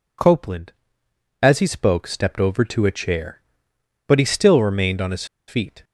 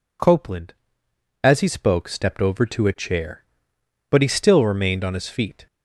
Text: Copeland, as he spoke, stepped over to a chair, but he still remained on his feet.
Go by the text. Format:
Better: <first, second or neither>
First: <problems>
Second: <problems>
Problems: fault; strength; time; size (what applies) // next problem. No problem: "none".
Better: second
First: pauses between "his" and "feet"; slight; at 5.2 s; 0.22 s long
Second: none